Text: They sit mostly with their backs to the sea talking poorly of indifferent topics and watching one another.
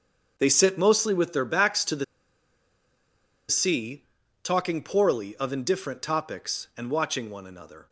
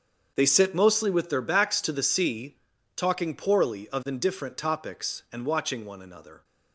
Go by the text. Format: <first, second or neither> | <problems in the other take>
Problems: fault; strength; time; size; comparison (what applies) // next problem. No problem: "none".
second | starts louder than the rest; until 1.3 s; 7 dB; also in the second // pauses between "the" and "sea"; strong; at 2.0 s; 1.4 s long // pauses between "sea" and "talking"; at 4.0 s; 0.38 s long; also in the second